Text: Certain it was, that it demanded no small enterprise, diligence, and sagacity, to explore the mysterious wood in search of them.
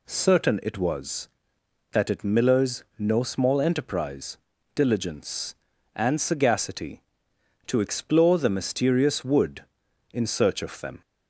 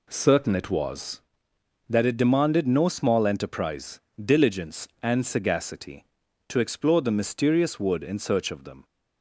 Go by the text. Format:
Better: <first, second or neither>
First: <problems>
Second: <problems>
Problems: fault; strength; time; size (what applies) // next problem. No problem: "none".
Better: second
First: says "millers" for "demanded"; at 2.2 s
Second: none